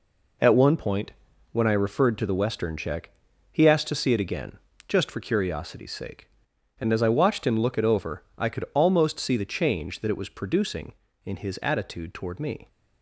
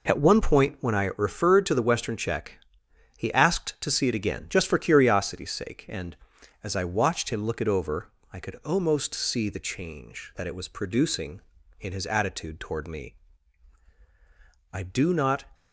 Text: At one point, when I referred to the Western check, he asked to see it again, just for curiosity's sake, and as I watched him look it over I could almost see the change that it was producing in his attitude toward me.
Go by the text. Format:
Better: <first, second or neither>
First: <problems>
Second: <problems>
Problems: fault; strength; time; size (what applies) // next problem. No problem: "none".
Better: first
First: none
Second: pauses between "over" and "I"; slight; at 8.1 s; 0.20 s long // goes on to say "I do not"; noticeable; from 14.7 s on; 0.72 s long